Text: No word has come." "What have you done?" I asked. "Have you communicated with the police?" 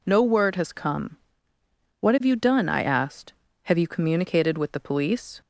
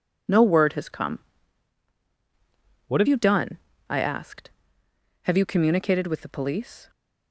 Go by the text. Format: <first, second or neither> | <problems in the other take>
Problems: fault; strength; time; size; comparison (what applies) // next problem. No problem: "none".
first | changes voice from "What" to "have"; from 2.8 to 3.0 s; 0.2 s long